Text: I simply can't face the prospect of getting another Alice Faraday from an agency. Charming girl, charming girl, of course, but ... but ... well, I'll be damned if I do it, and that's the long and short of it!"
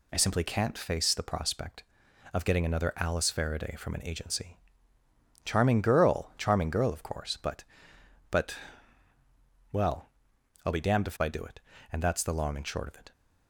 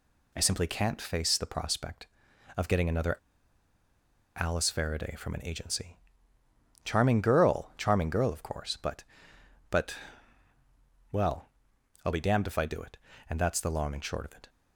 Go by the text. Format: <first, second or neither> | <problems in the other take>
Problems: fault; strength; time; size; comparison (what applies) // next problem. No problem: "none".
first | pauses between "another" and "Alice"; at 3.1 s; 1.2 s long